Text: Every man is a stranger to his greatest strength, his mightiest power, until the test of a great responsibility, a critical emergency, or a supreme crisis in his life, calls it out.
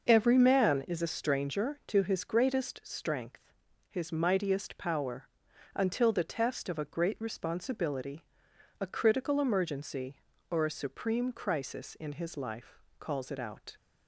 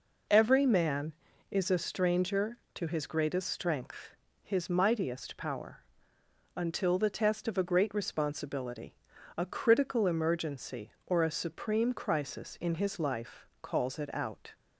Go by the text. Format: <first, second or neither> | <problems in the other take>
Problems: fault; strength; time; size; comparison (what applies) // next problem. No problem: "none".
neither | none